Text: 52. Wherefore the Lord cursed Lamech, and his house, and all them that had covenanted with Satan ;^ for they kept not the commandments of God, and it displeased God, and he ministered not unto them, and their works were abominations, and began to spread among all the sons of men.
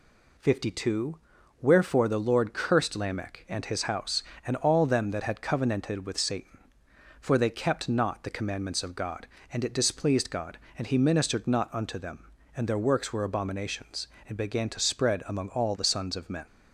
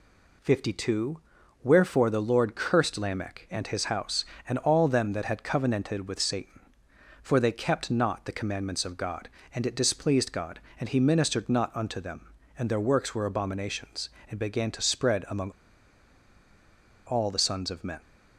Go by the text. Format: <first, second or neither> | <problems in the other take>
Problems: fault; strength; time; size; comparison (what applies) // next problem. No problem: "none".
first | pauses between "among" and "all"; strong; at 15.5 s; 1.5 s long